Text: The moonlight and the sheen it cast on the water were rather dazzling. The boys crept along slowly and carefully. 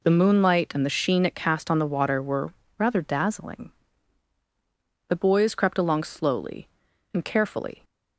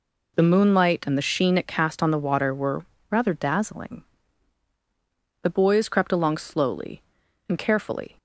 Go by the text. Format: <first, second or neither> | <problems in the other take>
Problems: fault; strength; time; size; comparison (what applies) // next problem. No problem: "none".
neither | pauses between "were" and "rather"; slight; the same in both